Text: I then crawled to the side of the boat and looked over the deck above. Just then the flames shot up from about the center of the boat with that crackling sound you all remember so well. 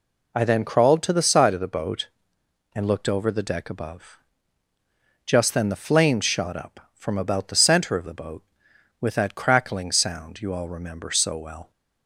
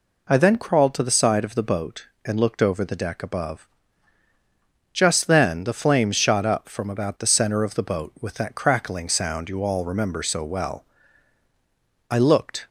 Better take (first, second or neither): first